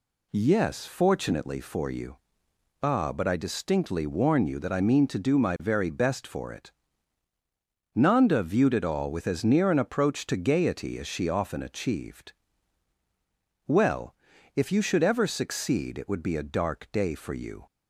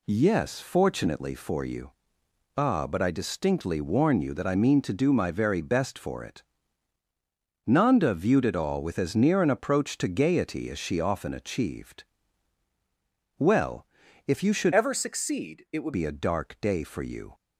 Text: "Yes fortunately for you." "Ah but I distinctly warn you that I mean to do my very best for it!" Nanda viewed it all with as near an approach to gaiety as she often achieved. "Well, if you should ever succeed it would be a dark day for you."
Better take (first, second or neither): first